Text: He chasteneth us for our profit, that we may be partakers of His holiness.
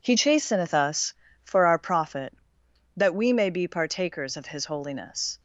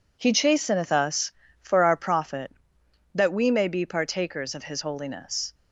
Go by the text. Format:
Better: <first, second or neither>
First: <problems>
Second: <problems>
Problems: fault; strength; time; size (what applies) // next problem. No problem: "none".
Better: neither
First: none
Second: none